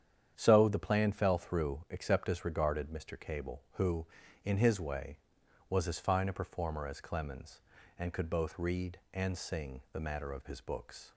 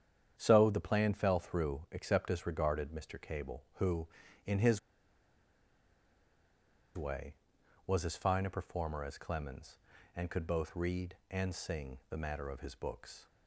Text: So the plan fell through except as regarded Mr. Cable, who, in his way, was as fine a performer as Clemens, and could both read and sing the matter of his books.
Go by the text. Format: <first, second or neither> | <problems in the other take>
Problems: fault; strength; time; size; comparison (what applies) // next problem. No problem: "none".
first | starts louder than the rest; strong; until 1.3 s; 9 dB; strong in the first // pauses between "his" and "way"; strong; at 4.7 s; 2.1 s long